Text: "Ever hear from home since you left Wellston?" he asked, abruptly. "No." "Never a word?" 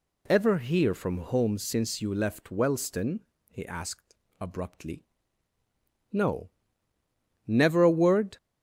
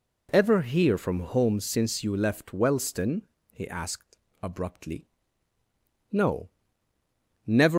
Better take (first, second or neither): first